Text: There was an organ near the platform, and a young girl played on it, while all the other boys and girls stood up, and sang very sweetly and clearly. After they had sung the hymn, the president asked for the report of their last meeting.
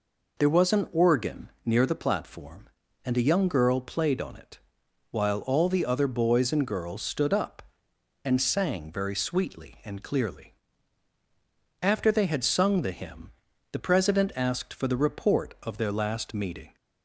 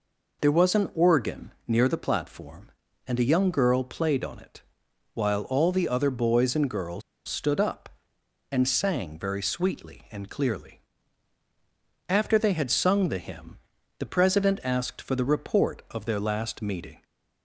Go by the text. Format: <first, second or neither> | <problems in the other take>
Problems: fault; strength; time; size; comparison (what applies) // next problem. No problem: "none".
first | pauses between "organ" and "near"; slight; at 1.5 s; 0.16 s long; slight in the first // pauses between "girls" and "stood"; slight; at 7.0 s; 0.25 s long